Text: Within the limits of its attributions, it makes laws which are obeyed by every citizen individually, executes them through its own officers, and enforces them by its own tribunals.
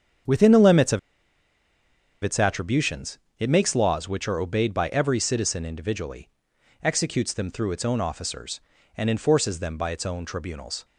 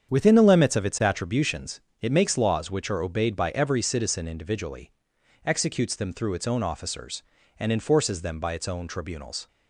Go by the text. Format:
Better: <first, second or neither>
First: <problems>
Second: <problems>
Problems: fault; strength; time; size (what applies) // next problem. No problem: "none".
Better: second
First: starts louder than the rest; strong; until 2.5 s; 8 dB // pauses between "of" and "its"; at 0.9 s; 1.2 s long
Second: starts louder than the rest; strong; until 1.1 s; 8 dB